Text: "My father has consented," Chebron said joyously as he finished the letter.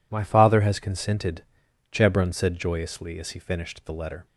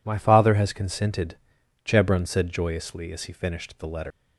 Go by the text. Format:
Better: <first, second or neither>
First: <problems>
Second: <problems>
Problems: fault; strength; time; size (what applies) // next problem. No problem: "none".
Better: first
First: none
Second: leaves "letter" unfinished; at 4.1 s; 95 ms